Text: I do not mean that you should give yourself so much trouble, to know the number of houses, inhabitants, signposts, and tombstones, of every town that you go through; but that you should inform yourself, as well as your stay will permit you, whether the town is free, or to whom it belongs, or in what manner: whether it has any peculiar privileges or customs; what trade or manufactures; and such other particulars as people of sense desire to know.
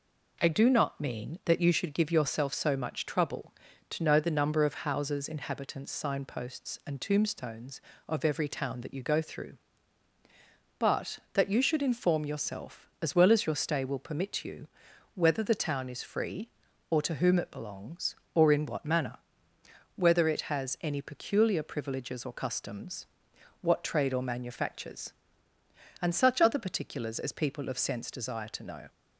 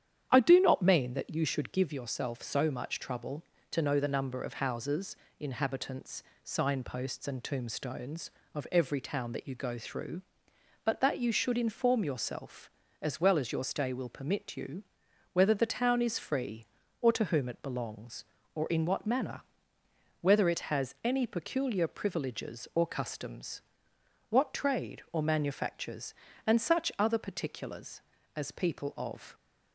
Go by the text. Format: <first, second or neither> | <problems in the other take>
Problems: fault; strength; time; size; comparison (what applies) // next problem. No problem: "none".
first | starts louder than the rest; strong; until 1.3 s; 9.5 dB // stops before "sense desire to know"; at 29.3 s